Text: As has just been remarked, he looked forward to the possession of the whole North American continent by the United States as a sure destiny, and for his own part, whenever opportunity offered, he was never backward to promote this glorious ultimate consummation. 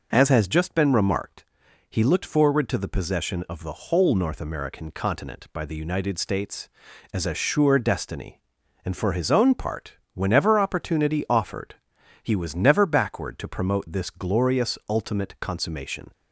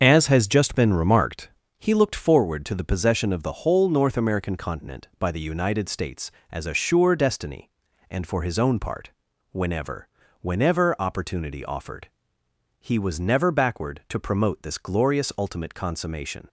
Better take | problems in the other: first | starts louder than the rest; until 1.0 s; 6.5 dB // says "whenever" twice; at 10.3 s

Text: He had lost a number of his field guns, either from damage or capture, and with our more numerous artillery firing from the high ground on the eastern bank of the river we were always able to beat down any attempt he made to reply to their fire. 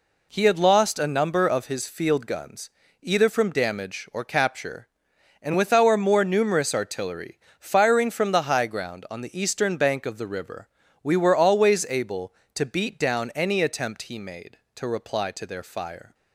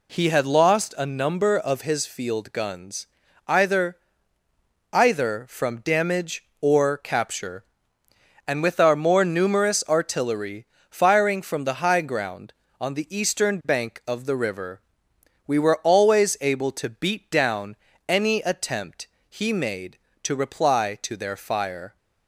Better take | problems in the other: first | says "either" twice; at 4.9 s // pauses between "artillery" and "firing"; slight; at 10.6 s; 0.24 s long; slight in the first // pauses between "river" and "we"; noticeable; at 14.7 s; 0.68 s long; slight in the first // pauses between "down" and "any"; slight; at 17.7 s; 0.34 s long // pauses between "attempt" and "he"; slight; at 19.0 s; 0.20 s long

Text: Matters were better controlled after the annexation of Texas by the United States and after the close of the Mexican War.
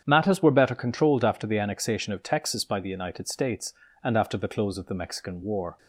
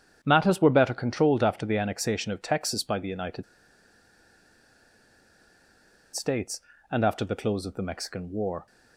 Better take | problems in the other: first | starts louder than the rest; strong; until 1.2 s; 8.5 dB; strong in the first // pauses between "United" and "States"; strong; at 3.4 s; 2.7 s long

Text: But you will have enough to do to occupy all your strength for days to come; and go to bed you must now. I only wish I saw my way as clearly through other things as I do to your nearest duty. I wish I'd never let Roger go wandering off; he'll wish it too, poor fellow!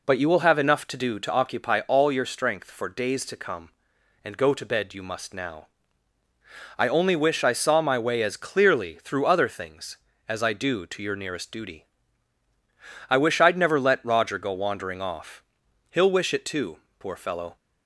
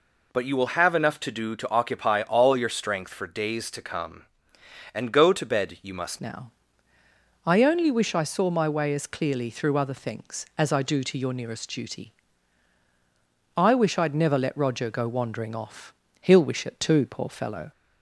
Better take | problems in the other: first | changes voice at "now"; from 6.2 s on; 11.5 s long

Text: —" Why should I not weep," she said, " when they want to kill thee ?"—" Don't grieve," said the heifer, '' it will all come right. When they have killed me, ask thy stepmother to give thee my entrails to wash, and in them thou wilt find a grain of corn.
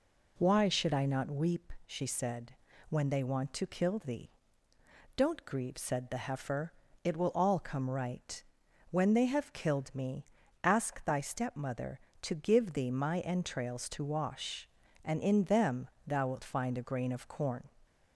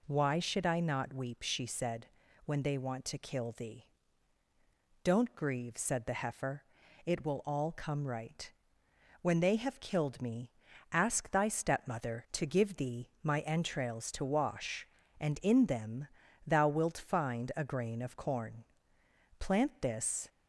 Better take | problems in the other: first | pauses between "them" and "thou"; at 16.0 s; 0.38 s long; slight in the first // goes on to say "Plant this"; noticeable; from 19.3 s on; 0.90 s long

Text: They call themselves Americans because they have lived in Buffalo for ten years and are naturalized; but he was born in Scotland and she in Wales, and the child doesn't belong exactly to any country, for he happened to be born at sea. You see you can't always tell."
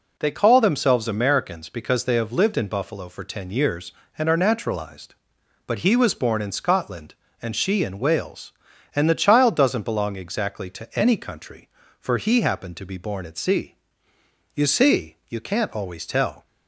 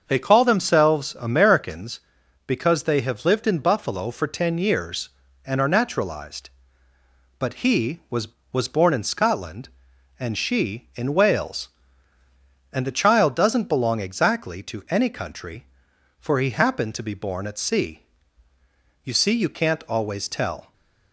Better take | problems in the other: first | starts louder than the rest; until 1.0 s; 6.5 dB // says "was" twice; at 8.5 s

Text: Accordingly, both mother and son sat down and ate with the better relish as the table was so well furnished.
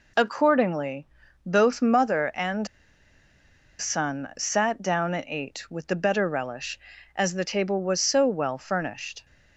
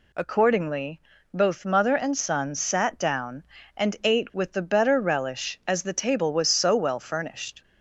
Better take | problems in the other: second | pauses between "and" and "son"; at 2.6 s; 1.1 s long

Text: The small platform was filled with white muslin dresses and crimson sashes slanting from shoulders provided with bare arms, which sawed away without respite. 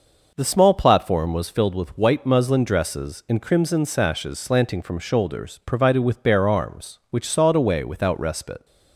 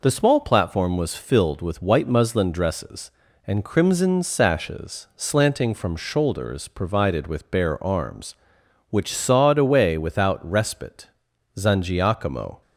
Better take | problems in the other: first | goes on to say "Zangiacomo"; noticeable; from 11.5 s on; 1.0 s long

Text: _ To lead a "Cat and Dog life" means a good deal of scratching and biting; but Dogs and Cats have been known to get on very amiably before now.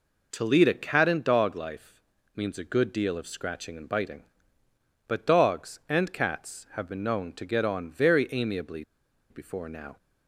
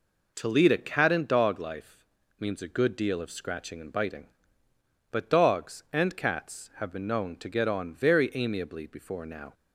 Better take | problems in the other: second | pauses between "life" and "means"; at 1.9 s; 0.42 s long; also in the second // pauses between "amiably" and "before"; noticeable; at 8.8 s; 0.47 s long

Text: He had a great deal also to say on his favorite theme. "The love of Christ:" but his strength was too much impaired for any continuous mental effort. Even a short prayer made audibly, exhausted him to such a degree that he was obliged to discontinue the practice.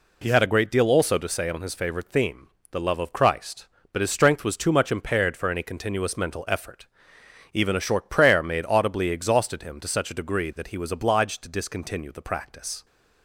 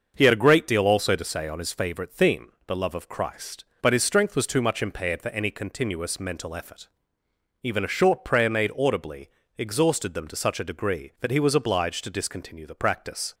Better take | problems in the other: first | starts louder than the rest; until 1.1 s; 6.5 dB // says "them" for "him"; at 10.1 s

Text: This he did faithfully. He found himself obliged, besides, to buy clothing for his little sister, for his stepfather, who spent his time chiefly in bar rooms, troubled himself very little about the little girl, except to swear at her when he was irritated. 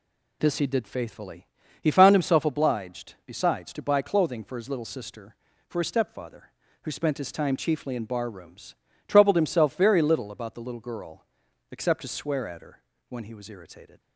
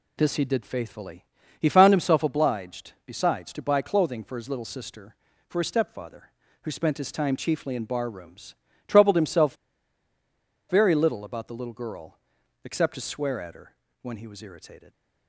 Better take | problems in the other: first | pauses between "himself" and "very"; at 9.5 s; 1.1 s long // pauses between "her" and "when"; slight; at 13.7 s; 0.28 s long; slight in the first

